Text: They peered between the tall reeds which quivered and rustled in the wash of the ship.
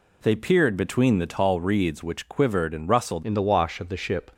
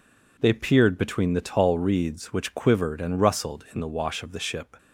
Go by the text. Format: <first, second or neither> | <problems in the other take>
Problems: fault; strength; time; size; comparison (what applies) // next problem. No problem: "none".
second | changes voice at "in"; from 3.2 s on; 1.0 s long